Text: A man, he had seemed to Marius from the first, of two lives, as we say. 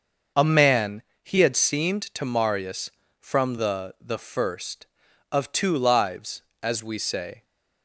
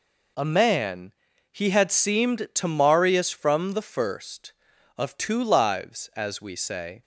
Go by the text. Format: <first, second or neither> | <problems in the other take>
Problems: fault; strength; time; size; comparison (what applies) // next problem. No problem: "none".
second | starts louder than the rest; until 1.5 s; 6 dB // says "the" twice; at 4.0 s